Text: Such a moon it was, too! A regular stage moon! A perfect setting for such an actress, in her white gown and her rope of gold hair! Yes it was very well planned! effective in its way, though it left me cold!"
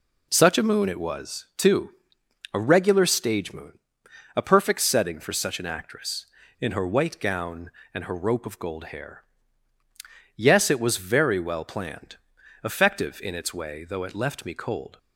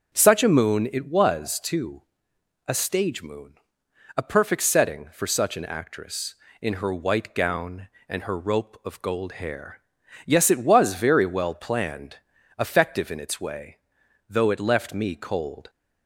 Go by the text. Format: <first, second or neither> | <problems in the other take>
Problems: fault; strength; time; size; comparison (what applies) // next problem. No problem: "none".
first | starts louder than the rest; until 1.1 s; 6.5 dB // skips "regular"; at 2.7 s